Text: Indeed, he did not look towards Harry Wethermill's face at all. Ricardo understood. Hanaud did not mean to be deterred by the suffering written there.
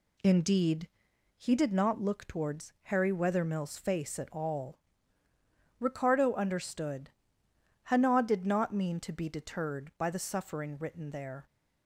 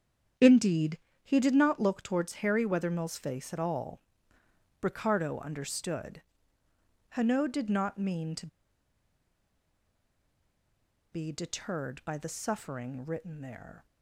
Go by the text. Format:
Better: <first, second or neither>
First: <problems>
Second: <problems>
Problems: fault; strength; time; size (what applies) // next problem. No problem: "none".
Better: first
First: none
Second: starts louder than the rest; strong; until 1.6 s; 8 dB // pauses between "to" and "be"; strong; at 8.4 s; 2.6 s long